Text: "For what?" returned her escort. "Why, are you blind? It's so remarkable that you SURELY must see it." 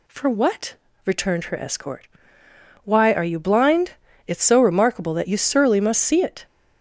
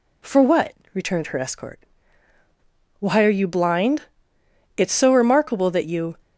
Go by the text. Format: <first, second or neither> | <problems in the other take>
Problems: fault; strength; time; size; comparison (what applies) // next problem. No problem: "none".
first | stops before "SURELY must see it"; at 6.2 s